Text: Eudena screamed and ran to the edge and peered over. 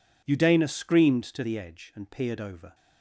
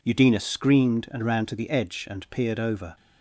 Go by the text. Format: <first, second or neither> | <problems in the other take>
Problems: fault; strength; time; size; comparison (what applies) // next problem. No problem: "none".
second | skips "and ran"; at 1.2 s